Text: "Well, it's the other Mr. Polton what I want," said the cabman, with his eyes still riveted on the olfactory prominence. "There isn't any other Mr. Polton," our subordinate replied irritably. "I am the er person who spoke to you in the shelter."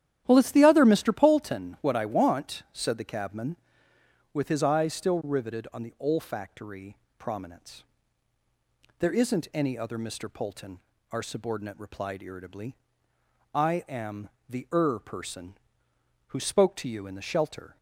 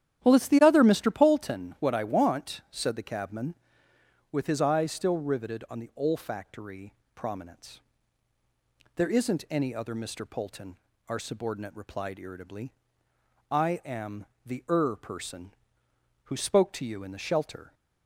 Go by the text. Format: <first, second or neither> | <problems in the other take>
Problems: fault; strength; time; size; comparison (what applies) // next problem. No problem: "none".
neither | starts louder than the rest; strong; the same in both // pauses between "olfactory" and "prominence"; slight; the same in both // pauses between "am" and "the"; slight; the same in both